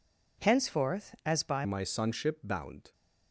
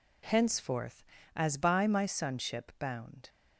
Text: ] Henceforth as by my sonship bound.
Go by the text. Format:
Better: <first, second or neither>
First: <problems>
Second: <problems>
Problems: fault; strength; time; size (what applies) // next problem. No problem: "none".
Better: second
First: changes voice at "my"; from 1.6 s on; 1.3 s long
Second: none